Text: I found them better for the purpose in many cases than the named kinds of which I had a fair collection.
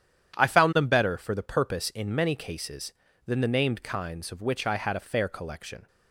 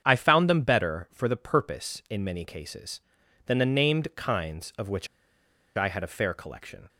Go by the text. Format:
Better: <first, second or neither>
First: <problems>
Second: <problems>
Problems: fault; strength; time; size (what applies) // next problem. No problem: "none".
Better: first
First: starts louder than the rest; strong; until 1.4 s; 9.5 dB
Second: starts louder than the rest; strong; until 1.0 s; 8 dB // pauses between "which" and "I"; noticeable; at 5.0 s; 0.71 s long